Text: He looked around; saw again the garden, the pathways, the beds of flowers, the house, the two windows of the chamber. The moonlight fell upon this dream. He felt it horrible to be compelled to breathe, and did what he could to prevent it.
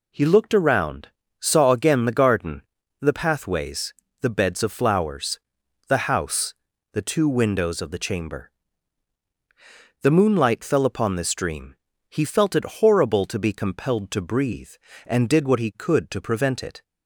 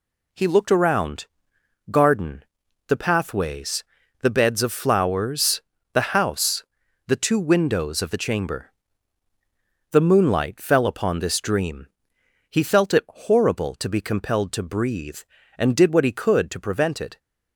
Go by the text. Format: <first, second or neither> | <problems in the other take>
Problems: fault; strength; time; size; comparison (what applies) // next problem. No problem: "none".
first | skips "saw again the"; at 1.5 s